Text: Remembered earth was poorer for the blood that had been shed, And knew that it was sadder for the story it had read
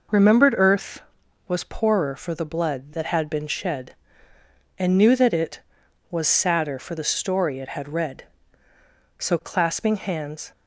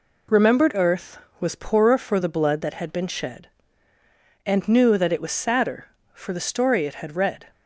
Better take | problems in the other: second | goes on to say "So clasping hands"; from 9.1 s on; 1.3 s long

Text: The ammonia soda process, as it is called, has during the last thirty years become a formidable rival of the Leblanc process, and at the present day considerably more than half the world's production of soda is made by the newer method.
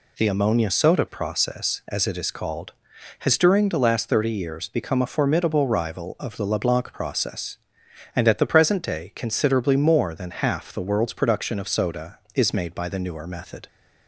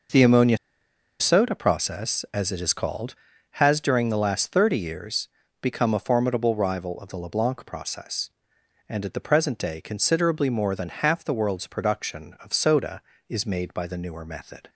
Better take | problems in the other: first | pauses between "ammonia" and "soda"; noticeable; at 0.5 s; 0.63 s long // pauses between "years" and "become"; slight; at 5.2 s; 0.32 s long

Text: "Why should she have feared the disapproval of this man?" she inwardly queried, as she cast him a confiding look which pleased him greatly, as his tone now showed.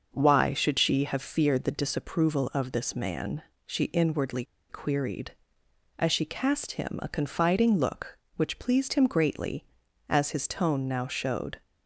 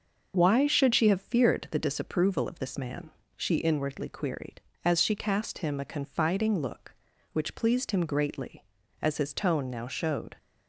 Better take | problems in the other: second | starts louder than the rest; until 1.1 s; 6 dB; also in the second // pauses between "inwardly" and "queried"; slight; at 4.4 s; 0.25 s long

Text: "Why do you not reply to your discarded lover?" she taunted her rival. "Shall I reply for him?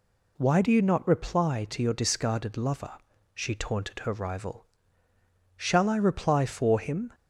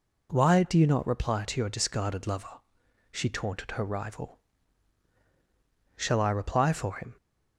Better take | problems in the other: neither | none

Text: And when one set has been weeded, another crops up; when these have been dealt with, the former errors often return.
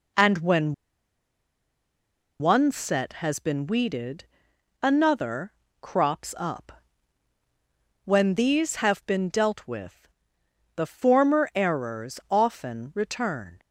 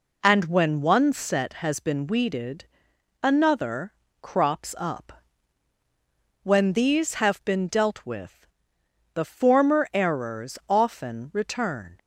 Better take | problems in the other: second | pauses between "when" and "one"; strong; at 0.7 s; 1.6 s long // pauses between "another" and "crops"; slight; at 5.5 s; 0.30 s long; slight in the second

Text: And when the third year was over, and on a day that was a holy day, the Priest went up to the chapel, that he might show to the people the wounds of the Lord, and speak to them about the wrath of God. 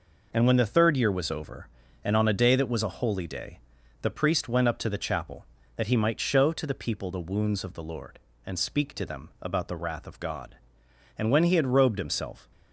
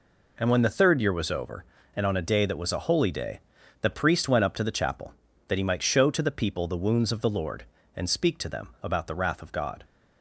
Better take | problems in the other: second | goes on to say "And when he had robed himself"; from 11.1 s on; 1.3 s long

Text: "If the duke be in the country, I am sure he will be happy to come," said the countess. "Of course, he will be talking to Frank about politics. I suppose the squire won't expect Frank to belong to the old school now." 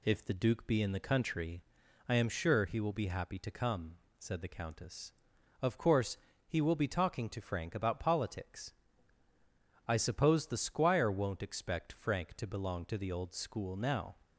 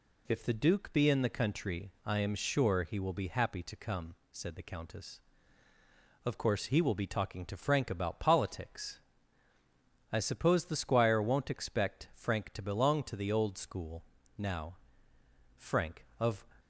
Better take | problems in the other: first | pauses between "school" and "now"; slight; at 14.0 s; 0.32 s long // goes on to say "Frank of"; noticeable; from 15.5 s on; 0.86 s long

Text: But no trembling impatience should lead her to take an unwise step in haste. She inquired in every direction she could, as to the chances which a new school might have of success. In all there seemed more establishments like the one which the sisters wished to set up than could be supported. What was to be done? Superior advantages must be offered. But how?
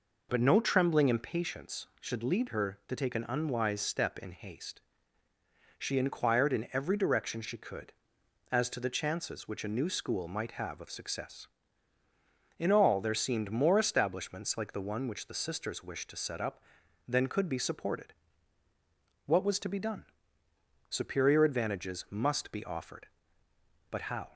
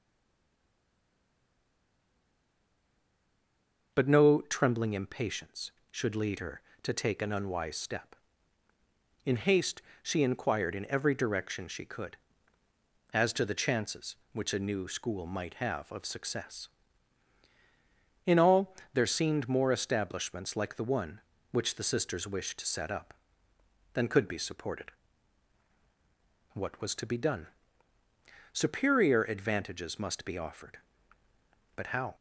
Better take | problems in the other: first | stays silent before the first word; strong; until 3.9 s; 3.9 s long // pauses between "all" and "there"; slight; at 18.7 s; 0.20 s long

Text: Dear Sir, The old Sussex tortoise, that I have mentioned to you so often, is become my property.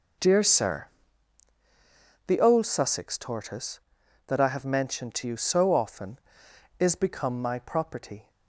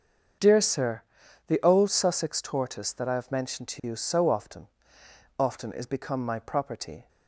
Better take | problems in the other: first | starts louder than the rest; until 1.8 s; 7 dB // says "often" twice; at 5.3 s

